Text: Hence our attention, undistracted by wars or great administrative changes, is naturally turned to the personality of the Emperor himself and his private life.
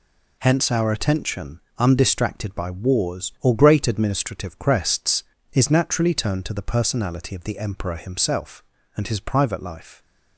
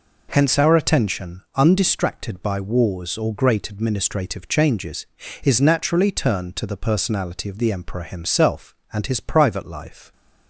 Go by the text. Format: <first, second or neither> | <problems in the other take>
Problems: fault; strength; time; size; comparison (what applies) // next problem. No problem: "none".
second | says "crests" for "changes"; at 4.5 s